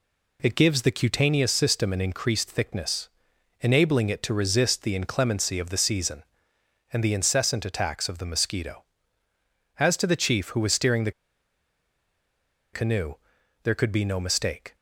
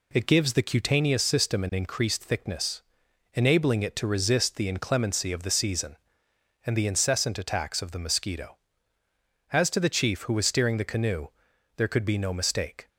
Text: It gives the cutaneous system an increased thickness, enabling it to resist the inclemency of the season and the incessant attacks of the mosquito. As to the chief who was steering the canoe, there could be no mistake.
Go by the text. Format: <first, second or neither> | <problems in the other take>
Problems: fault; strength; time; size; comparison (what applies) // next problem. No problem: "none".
second | pauses between "the" and "canoe"; strong; at 11.1 s; 1.6 s long